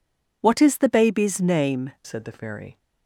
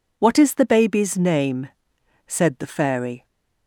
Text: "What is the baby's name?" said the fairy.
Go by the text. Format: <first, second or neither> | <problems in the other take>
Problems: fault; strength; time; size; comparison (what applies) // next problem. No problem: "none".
second | changes voice at "said"; from 2.0 s on; 0.7 s long